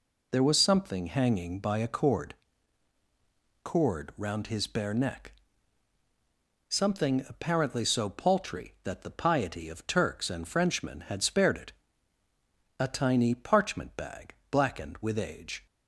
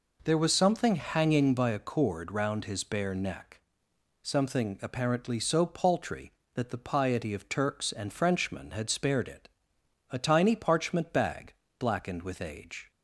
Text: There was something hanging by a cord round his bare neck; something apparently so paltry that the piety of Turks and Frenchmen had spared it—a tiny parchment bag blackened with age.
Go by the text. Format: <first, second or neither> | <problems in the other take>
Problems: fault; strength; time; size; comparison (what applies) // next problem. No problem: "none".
second | says "cord" twice; at 3.6 s // pauses between "bag" and "blackened"; slight; at 14.3 s; 0.16 s long; slight in the second